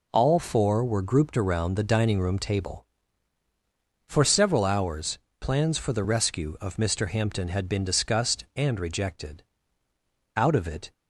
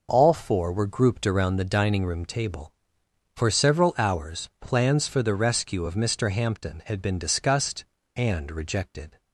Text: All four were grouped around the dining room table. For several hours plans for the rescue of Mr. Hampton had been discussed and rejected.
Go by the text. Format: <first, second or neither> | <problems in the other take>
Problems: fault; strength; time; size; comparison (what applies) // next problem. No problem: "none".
second | pauses between "hours" and "plans"; slight; at 5.1 s; 0.20 s long // goes on to say "Out of it"; from 10.3 s on; 0.58 s long